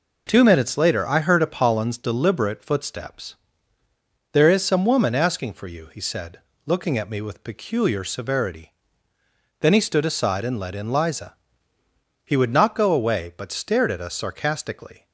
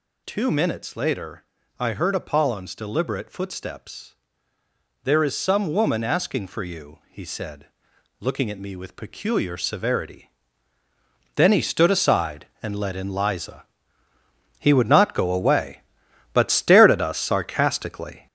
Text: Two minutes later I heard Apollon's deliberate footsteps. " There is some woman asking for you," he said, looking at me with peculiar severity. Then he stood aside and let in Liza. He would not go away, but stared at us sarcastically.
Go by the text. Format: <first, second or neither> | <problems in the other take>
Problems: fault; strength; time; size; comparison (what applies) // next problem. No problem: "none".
first | gets louder; strong; throughout; 8 dB // pauses between "later" and "I"; slight; at 1.4 s; 0.34 s long